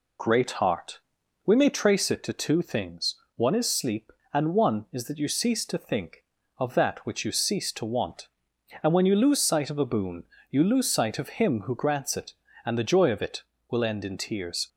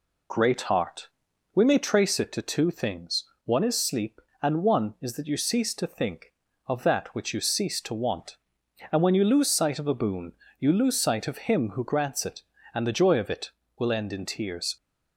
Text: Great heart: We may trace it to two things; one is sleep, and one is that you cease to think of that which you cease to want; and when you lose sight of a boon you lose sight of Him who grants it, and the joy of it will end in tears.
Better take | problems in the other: neither | pauses between "boon" and "you"; slight; the same in both

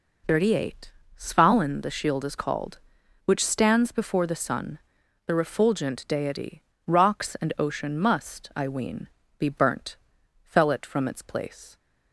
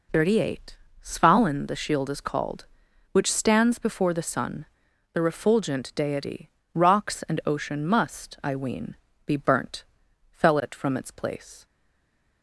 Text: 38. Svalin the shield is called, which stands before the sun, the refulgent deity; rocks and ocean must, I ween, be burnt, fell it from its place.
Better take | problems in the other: first | stays silent after the last word; slight; from 11.6 s on; 0.8 s long

